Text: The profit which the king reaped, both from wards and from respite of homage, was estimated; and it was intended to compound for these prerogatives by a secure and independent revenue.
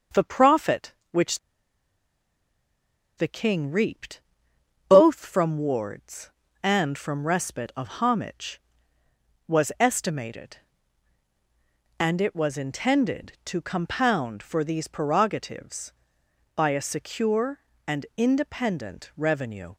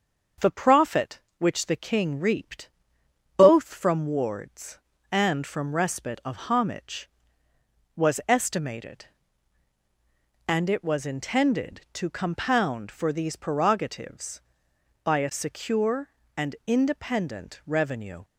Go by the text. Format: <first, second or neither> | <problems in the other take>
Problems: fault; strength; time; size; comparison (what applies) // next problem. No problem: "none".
second | starts louder than the rest; until 1.3 s; 6.5 dB; also in the second // pauses between "which" and "the"; strong; at 1.3 s; 1.7 s long